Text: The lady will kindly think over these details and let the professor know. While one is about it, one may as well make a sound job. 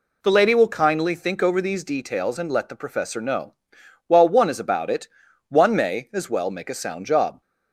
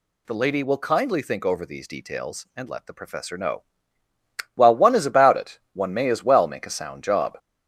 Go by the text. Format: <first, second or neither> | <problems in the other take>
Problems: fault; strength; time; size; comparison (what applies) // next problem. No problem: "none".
first | gets louder; slight; throughout; 3 dB